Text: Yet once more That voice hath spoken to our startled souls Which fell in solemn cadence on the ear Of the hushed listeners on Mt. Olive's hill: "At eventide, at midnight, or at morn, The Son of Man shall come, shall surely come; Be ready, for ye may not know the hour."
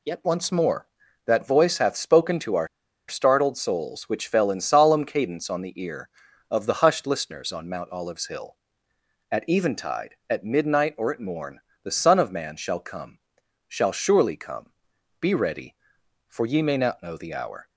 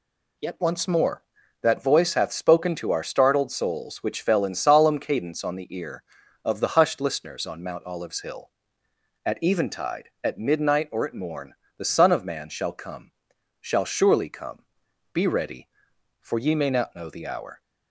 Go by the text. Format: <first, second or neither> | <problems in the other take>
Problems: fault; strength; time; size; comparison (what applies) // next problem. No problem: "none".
second | pauses between "our" and "startled"; at 2.6 s; 0.41 s long